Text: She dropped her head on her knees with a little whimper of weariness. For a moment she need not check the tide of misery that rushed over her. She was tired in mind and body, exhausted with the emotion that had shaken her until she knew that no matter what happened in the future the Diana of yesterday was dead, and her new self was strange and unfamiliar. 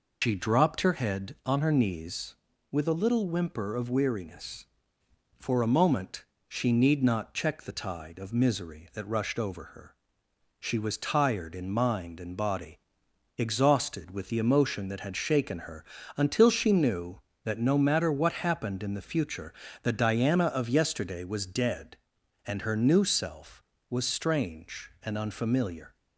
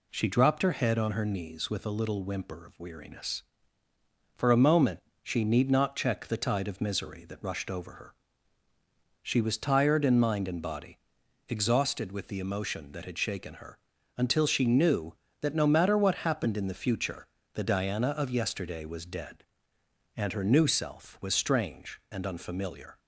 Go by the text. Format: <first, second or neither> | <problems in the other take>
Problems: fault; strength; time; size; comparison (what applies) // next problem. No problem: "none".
second | loses the start of "She"; at 0.2 s; 130 ms // pauses between "moment" and "she"; slight; at 6.2 s; 0.24 s long; slight in the second // pauses between "her" and "until"; slight; at 15.8 s; 0.32 s long; also in the second // pauses between "future" and "the"; slight; at 19.5 s; 0.30 s long; slight in the second